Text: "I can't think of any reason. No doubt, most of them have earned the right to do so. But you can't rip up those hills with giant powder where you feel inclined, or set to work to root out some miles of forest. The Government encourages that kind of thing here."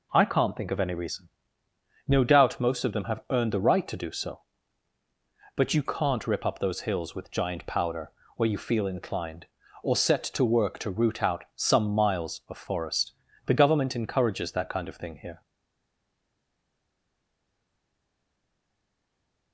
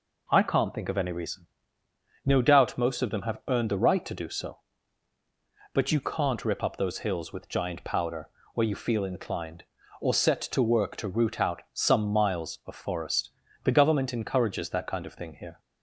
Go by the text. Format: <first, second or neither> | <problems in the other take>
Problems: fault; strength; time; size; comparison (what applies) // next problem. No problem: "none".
second | pauses between "powder" and "where"; slight; at 8.1 s; 0.24 s long; slight in the second // stays silent after the last word; strong; from 15.4 s on; 4.1 s long